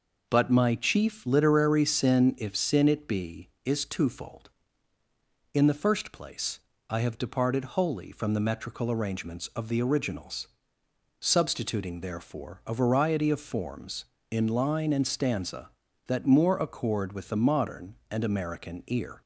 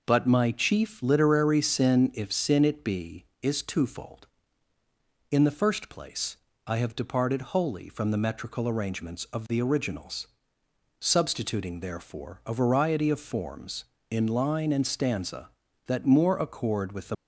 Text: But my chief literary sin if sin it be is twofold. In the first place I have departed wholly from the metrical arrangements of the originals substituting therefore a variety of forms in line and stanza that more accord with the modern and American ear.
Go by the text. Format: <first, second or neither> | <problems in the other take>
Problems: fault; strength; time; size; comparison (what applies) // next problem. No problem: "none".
first | pauses between "place" and "I"; slight; at 6.3 s; 0.30 s long; slight in the first // pauses between "originals" and "substituting"; noticeable; at 10.2 s; 0.72 s long; noticeable in the first // stops before "modern and American ear"; at 17.1 s